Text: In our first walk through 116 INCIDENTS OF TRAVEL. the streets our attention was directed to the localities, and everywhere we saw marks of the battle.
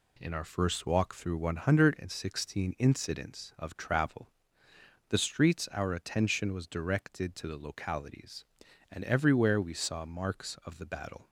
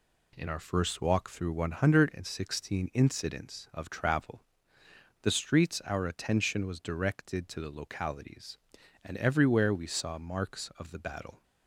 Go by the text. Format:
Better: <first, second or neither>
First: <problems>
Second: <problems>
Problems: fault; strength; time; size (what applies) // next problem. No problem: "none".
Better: neither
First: none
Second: none